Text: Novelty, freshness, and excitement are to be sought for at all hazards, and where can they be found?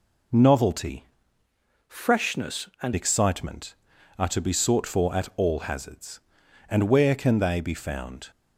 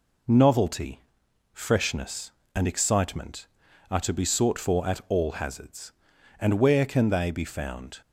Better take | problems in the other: second | changes voice from "freshness" to "and"; from 1.8 to 2.9 s; 1.1 s long

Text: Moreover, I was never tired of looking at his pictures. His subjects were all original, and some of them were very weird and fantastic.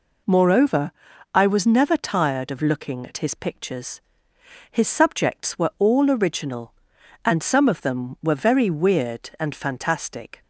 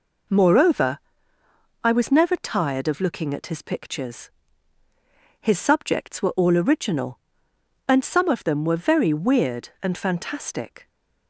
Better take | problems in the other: neither | none

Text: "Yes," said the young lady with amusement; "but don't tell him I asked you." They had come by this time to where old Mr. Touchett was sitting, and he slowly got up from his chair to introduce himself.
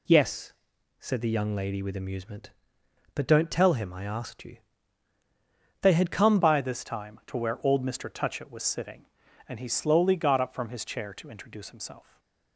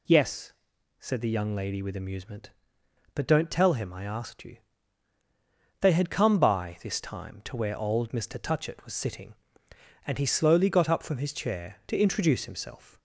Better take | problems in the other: second | changes voice at "by"; from 6.3 s on; 5.8 s long // stays silent after the last word; slight; from 12.0 s on; 0.5 s long

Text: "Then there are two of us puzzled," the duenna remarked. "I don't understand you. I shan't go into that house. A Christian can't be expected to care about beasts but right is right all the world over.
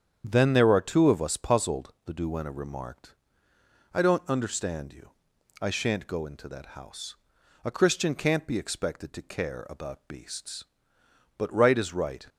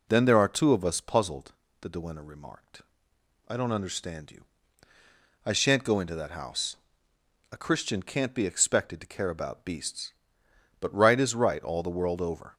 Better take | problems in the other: second | starts louder than the rest; strong; until 1.3 s; 8.5 dB // stops before "all the world over"; at 12.2 s

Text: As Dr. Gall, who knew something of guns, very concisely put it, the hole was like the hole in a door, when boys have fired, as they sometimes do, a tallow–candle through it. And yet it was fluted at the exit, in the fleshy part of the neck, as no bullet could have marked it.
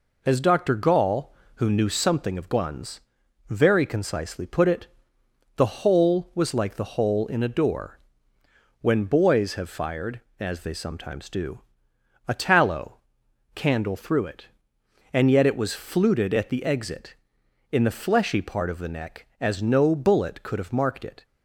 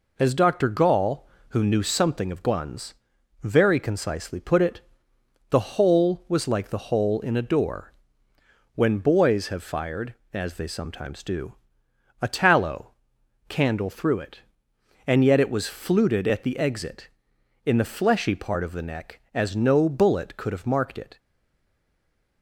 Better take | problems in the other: first | stays silent after the last word; noticeable; from 21.1 s on; 1.3 s long

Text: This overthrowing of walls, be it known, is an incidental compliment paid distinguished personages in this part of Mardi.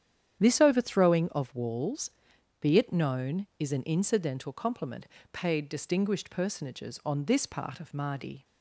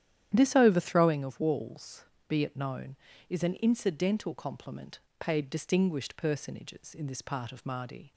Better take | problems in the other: second | starts louder than the rest; strong; until 1.4 s; 9.5 dB; strong in the second // pauses between "compliment" and "paid"; slight; at 5.0 s; 0.26 s long; slight in the second // says "on" for "in"; at 7.0 s

